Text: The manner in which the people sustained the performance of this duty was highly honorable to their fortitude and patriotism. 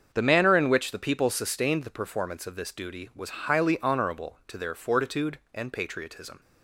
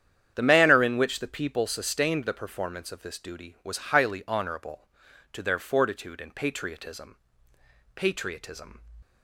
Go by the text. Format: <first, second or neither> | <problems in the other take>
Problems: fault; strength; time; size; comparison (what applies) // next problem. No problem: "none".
first | starts louder than the rest; strong; until 1.3 s; 9 dB; also in the first // says "patriotism" twice; at 7.9 s